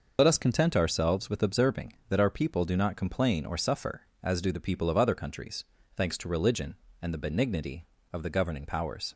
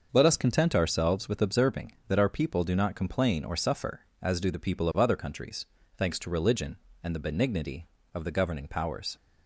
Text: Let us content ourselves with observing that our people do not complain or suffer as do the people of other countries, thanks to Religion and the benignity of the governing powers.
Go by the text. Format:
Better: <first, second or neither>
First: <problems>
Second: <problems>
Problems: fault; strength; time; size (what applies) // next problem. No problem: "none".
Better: second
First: loses the start of "Let"; at 0.1 s; 65 ms // starts louder than the rest; noticeable; until 1.1 s; 6 dB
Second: starts louder than the rest; until 1.1 s; 6.5 dB